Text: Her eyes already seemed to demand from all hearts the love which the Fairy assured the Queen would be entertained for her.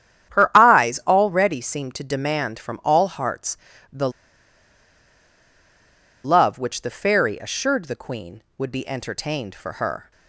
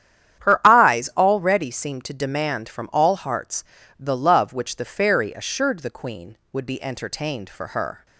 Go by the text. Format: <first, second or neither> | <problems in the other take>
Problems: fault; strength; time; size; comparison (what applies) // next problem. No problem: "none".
second | starts louder than the rest; strong; until 1.4 s; 10 dB; strong in the second // pauses between "hearts" and "the"; slight; at 3.5 s; 0.34 s long; slight in the second // pauses between "the" and "love"; strong; at 4.1 s; 2.1 s long